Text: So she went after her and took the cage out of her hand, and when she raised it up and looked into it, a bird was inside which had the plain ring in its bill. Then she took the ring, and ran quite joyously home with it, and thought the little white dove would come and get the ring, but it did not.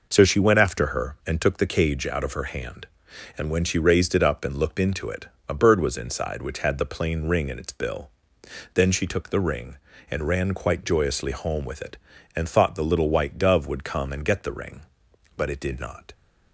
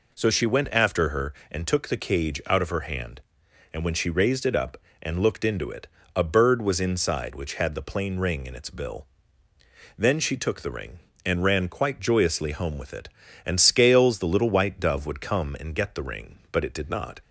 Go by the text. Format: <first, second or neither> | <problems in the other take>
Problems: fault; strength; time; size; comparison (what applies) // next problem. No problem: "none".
first | says "scales" for "thought"; at 13.6 s